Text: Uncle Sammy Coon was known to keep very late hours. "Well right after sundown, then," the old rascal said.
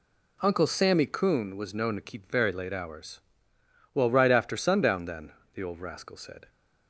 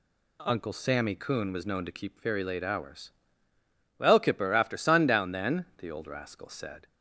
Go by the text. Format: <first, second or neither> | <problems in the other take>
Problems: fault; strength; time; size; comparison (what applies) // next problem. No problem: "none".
first | says "kipper" for "right"; at 4.1 s